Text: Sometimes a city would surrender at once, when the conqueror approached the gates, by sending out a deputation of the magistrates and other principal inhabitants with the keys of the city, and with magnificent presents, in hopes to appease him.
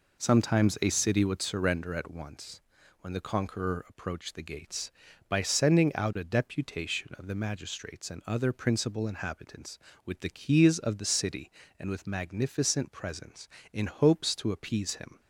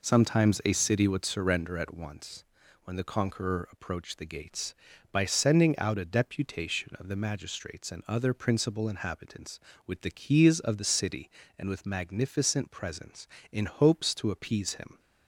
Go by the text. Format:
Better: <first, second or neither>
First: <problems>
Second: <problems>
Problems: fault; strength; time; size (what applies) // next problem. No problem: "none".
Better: neither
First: none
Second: none